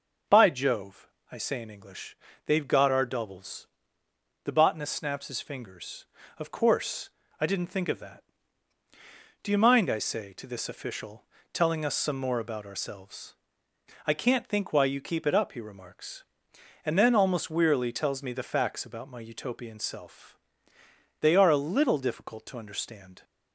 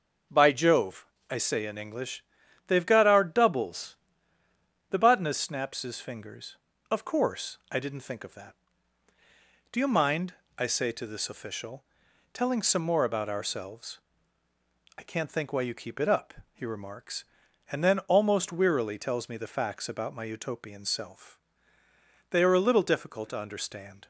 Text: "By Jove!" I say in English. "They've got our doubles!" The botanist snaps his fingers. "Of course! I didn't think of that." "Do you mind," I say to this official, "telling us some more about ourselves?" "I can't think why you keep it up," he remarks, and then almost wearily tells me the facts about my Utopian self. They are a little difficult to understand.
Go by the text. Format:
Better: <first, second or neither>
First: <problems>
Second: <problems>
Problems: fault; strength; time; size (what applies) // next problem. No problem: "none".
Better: first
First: none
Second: skips "us"; at 12.6 s